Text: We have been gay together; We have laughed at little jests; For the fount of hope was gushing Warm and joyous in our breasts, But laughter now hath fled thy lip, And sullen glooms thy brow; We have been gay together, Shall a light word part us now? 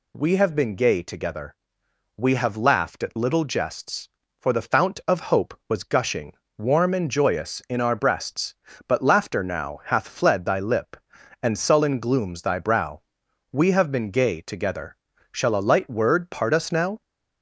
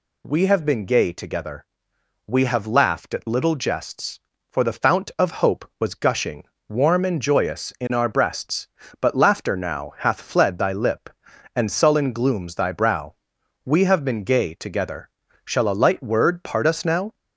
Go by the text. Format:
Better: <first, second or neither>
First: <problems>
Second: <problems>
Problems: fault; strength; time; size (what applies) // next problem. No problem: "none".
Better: neither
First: pauses between "gushing" and "Warm"; slight; at 6.3 s; 0.24 s long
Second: pauses between "gushing" and "Warm"; slight; at 6.4 s; 0.24 s long